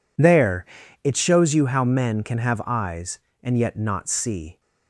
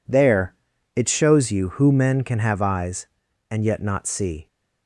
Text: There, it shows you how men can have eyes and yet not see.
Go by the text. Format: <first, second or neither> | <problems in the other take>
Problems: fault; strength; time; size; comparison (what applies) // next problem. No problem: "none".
first | says "who" for "how"; at 1.7 s